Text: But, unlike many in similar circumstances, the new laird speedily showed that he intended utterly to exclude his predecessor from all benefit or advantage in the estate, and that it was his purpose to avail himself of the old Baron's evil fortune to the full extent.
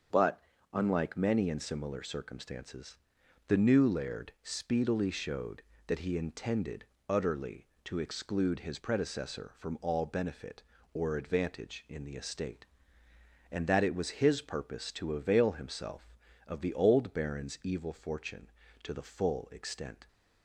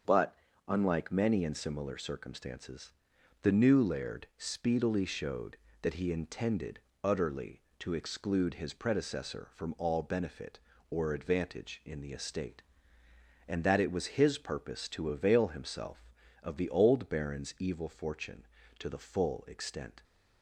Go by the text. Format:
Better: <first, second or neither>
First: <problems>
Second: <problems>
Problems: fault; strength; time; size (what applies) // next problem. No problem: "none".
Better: neither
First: starts louder than the rest; until 1.4 s; 7 dB // pauses between "intended" and "utterly"; slight; at 6.8 s; 0.22 s long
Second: starts louder than the rest; until 1.3 s; 7 dB // pauses between "intended" and "utterly"; slight; at 6.7 s; 0.22 s long